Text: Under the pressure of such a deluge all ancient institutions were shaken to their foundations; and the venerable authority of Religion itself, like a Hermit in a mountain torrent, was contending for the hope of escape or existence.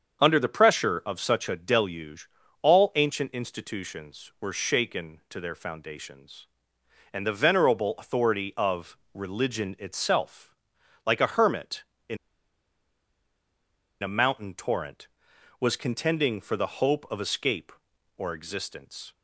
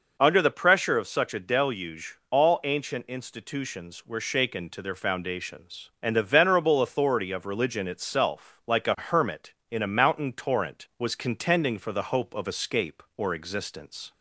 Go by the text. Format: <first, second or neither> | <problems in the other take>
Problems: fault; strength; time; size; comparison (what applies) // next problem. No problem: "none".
second | starts louder than the rest; until 1.2 s; 7 dB // pauses between "deluge" and "all"; slight; at 2.2 s; 0.34 s long // pauses between "of" and "Religion"; slight; at 8.9 s; 0.16 s long // pauses between "in" and "a"; strong; at 12.1 s; 1.8 s long